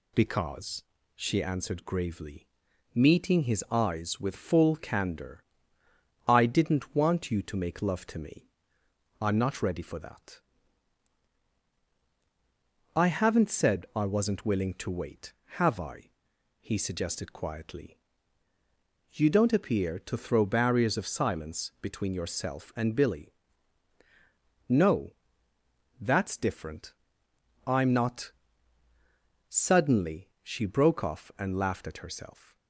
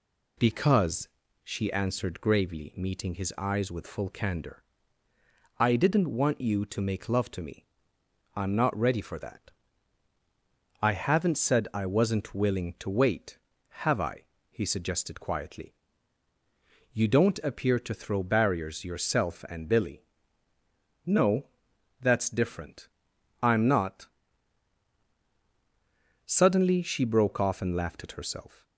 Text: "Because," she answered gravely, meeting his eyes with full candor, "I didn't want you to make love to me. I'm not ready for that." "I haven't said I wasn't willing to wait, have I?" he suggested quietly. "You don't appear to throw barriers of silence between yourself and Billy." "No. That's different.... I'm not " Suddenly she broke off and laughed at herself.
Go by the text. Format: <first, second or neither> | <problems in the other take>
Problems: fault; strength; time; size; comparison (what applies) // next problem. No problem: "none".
first | skips "of silence between"; at 18.8 s